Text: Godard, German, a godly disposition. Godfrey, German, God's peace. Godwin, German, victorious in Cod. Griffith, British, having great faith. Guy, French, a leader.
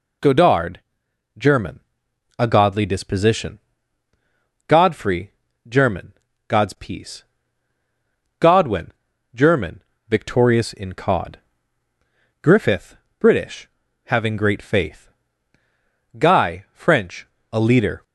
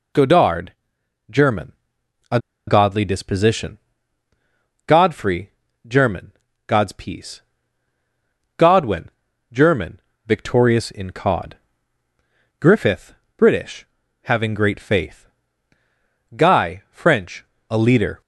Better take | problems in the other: first | pauses between "a" and "godly"; slight; at 2.3 s; 0.29 s long

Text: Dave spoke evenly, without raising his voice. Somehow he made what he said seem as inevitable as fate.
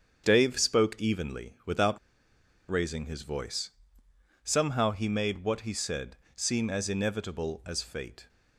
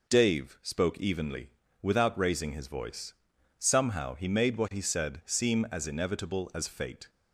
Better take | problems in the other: second | starts louder than the rest; strong; until 1.2 s; 7.5 dB // pauses between "without" and "raising"; noticeable; at 1.9 s; 0.71 s long // pauses between "said" and "seem"; slight; at 6.1 s; 0.20 s long

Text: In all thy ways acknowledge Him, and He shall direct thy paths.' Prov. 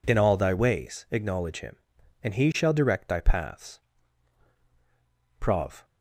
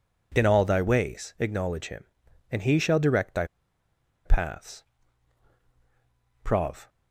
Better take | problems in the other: first | pauses between "thy" and "paths"; noticeable; at 3.4 s; 0.80 s long

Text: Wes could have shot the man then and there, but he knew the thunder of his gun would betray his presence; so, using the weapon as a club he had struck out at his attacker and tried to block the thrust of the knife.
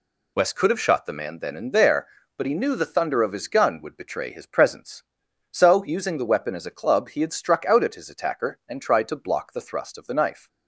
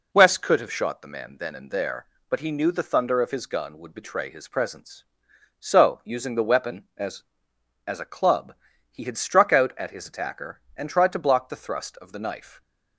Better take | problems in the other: first | says "as" twice; at 7.8 s // pauses between "club" and "he"; slight; at 8.5 s; 0.36 s long

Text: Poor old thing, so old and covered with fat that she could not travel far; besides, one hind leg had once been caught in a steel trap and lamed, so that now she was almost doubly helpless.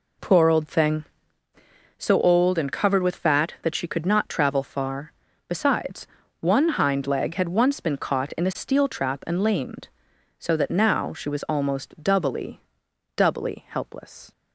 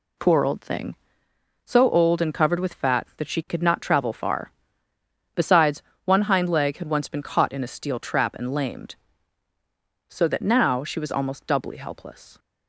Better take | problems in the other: second | says "doubly" twice; at 13.1 s

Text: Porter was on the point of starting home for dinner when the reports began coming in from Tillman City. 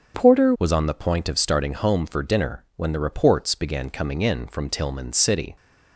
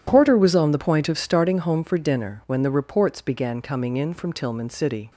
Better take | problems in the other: second | starts louder than the rest; strong; until 1.2 s; 7 dB // changes voice at "was"; from 0.5 s on; 5.0 s long

